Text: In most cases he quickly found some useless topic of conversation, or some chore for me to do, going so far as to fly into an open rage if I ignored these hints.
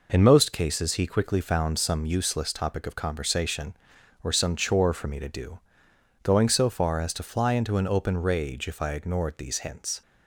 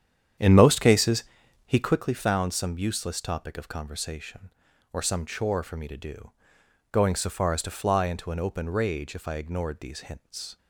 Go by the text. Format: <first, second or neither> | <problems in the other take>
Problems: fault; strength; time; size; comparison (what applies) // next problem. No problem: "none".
first | starts louder than the rest; strong; until 2.1 s; 9 dB // pauses between "cases" and "he"; at 1.2 s; 0.42 s long